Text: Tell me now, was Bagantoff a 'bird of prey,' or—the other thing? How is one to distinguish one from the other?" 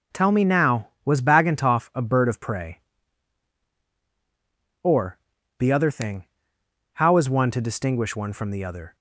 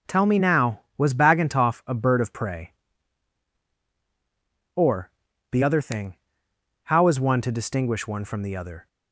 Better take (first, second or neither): neither